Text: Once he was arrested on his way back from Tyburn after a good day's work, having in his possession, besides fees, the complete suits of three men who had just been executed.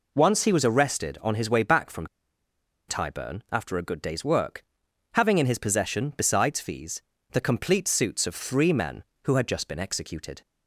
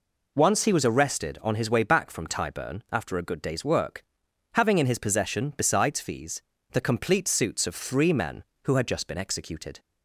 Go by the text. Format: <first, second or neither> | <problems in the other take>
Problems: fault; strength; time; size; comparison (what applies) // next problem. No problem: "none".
second | pauses between "from" and "Tyburn"; noticeable; at 2.0 s; 0.81 s long